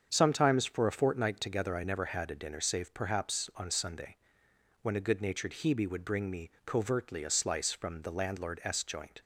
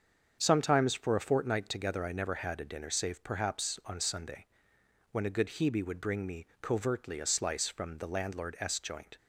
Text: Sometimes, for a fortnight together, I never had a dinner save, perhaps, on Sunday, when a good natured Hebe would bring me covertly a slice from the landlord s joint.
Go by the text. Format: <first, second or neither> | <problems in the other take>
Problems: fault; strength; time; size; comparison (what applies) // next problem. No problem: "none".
first | starts louder than the rest; until 1.4 s; 7 dB; also in the first // skips "natured"; at 5.4 s // pauses between "me" and "covertly"; slight; at 6.4 s; 0.16 s long; slight in the first